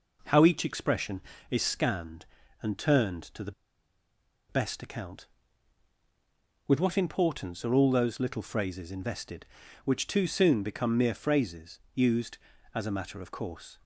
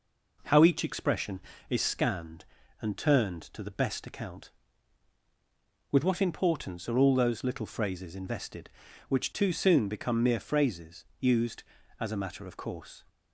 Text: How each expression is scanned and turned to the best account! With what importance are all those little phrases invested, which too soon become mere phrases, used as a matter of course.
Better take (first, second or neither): second